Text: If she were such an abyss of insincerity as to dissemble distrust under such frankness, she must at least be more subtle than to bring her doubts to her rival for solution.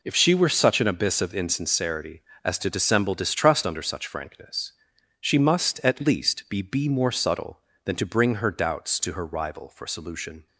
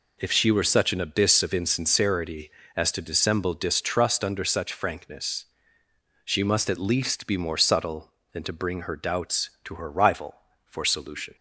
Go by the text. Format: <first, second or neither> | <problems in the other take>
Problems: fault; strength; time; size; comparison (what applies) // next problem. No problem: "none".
second | says "be" twice; at 6.6 s